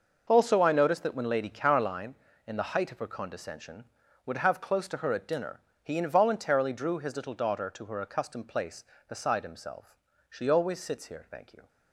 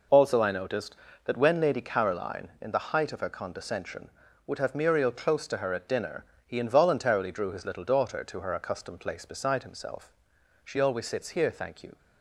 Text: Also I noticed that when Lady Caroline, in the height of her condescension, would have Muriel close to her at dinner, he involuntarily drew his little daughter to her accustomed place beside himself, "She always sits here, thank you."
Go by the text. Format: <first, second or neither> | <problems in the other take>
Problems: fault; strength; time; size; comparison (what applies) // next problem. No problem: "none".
second | skips "Muriel"; at 4.5 s